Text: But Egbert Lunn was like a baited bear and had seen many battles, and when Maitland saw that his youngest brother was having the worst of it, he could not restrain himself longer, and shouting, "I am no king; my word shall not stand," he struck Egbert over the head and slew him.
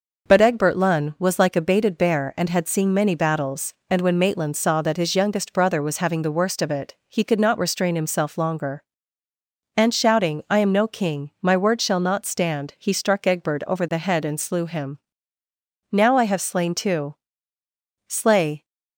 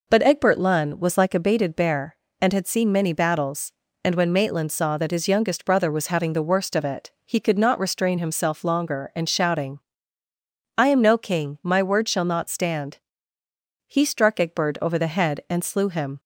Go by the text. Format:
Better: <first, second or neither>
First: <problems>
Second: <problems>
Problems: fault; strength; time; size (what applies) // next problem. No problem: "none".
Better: second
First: goes on to say "Now I have slain two slay"; strong; from 15.9 s on; 2.7 s long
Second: none